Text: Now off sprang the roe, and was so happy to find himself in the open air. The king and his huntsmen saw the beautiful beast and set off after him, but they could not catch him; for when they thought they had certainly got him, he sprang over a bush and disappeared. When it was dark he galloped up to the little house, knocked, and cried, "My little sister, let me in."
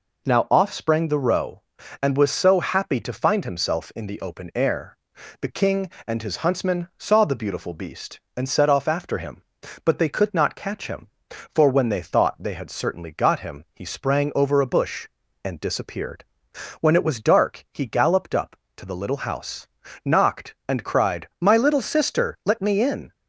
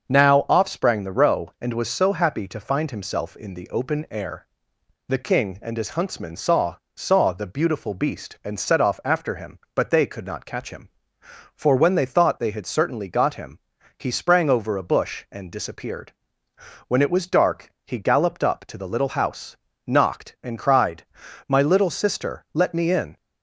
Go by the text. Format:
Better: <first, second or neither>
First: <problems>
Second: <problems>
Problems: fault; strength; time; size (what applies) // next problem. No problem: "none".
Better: first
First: none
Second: starts louder than the rest; until 1.1 s; 6.5 dB // says "saw" twice; at 6.9 s